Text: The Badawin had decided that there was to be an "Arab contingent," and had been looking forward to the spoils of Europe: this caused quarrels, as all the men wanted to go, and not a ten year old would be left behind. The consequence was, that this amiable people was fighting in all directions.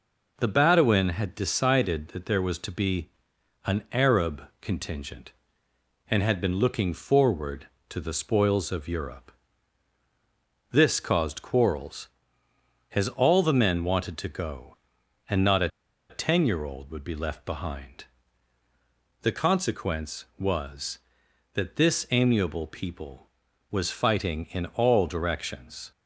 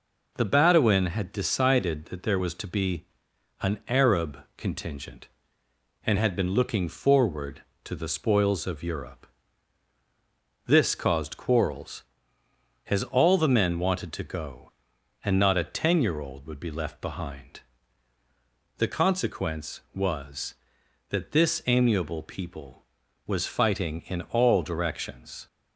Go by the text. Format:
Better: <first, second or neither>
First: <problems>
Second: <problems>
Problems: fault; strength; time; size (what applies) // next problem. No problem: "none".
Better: second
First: pauses between "be" and "an"; noticeable; at 3.0 s; 0.56 s long // pauses between "a" and "ten"; at 15.6 s; 0.41 s long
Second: pauses between "be" and "an"; noticeable; at 3.0 s; 0.56 s long